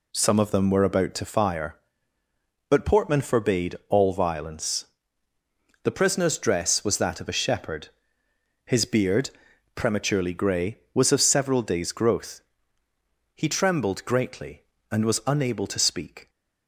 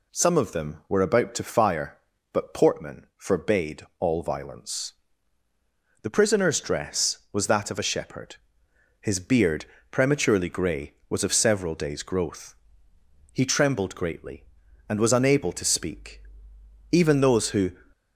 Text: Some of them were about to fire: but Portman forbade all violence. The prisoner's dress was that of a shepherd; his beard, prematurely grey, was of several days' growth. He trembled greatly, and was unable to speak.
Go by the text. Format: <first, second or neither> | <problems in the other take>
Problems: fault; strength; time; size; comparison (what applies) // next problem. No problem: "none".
first | pauses between "forbade" and "all"; slight; at 3.8 s; 0.18 s long // goes on to say "Even those who"; noticeable; from 16.9 s on; 0.80 s long